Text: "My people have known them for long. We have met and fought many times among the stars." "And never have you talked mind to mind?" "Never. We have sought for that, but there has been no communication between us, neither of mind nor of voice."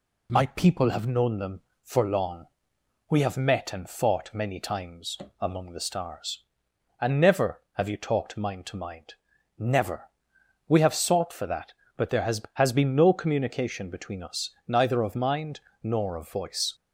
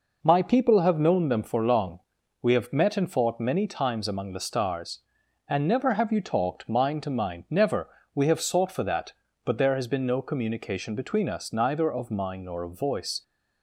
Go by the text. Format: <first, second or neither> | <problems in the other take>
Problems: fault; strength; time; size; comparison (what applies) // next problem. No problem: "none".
second | pauses between "times" and "among"; slight; at 5.1 s; 0.24 s long // says "has" twice; at 12.5 s // pauses between "mind" and "nor"; slight; at 15.5 s; 0.24 s long